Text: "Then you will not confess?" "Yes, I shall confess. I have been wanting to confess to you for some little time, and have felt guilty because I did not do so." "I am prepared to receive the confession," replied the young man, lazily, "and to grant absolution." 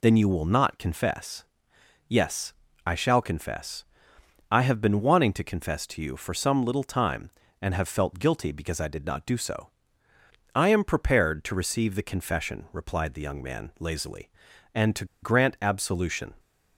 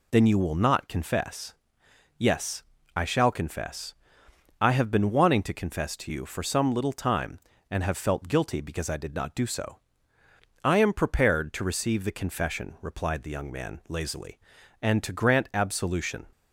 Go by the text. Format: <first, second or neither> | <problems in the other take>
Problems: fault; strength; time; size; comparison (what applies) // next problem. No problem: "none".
second | pauses between "to" and "grant"; slight; at 15.0 s; 0.18 s long